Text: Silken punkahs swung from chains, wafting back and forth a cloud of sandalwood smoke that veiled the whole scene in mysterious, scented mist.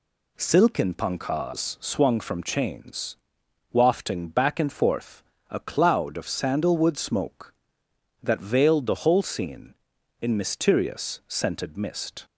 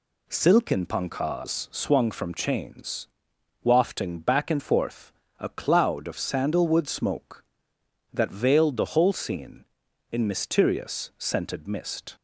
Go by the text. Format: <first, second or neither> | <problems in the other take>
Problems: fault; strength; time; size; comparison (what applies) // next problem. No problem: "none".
neither | pauses between "forth" and "a"; slight; the same in both